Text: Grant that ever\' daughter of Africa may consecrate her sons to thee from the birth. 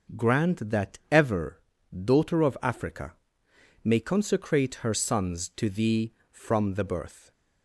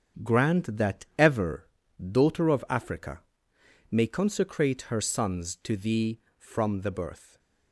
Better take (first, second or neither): first